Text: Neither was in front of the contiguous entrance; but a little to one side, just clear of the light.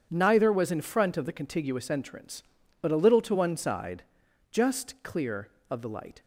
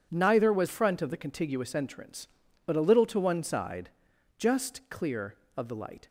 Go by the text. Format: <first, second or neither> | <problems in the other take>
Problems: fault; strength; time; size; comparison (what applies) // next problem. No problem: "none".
first | skips "in"; at 0.6 s